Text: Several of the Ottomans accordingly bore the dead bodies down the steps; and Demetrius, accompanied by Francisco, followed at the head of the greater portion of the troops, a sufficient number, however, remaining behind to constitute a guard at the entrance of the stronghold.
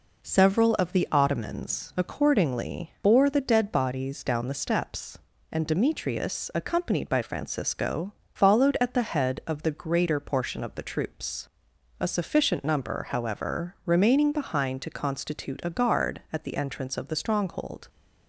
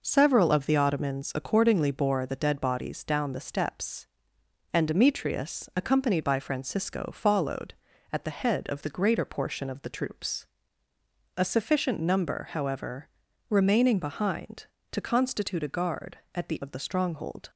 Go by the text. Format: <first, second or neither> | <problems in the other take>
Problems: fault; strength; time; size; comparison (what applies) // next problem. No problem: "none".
first | skips "entrance"; at 16.6 s